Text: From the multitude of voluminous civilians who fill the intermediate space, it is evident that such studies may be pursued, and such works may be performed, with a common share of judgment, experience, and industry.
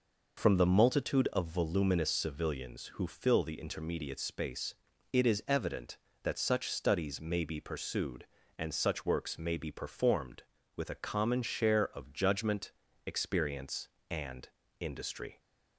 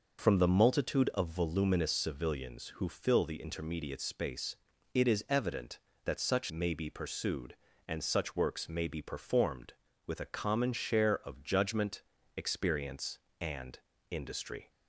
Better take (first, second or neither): first